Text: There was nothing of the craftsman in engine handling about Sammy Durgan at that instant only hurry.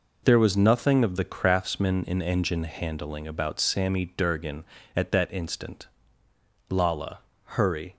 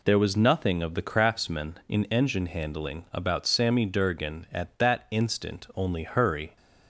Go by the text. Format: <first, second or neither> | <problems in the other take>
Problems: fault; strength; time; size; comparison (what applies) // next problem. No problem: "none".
second | says "lala" for "only"; at 6.7 s